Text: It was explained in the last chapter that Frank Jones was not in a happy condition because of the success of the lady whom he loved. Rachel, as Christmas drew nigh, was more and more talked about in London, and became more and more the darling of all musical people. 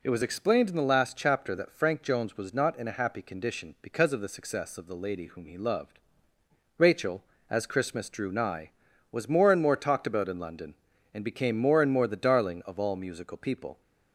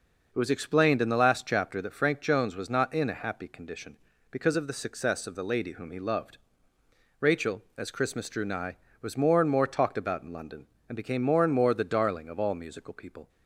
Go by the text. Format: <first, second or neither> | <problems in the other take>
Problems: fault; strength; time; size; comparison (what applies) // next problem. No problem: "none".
neither | none